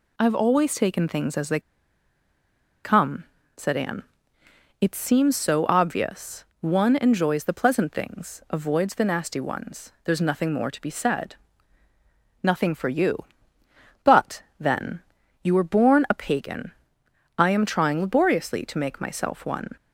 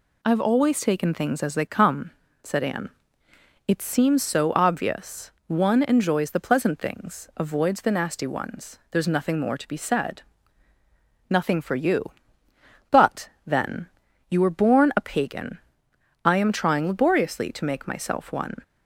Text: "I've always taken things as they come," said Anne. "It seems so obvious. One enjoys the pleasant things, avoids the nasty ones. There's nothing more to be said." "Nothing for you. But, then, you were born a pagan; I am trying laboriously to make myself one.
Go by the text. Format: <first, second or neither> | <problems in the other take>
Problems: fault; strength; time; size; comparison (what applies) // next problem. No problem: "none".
second | pauses between "they" and "come"; at 1.5 s; 1.2 s long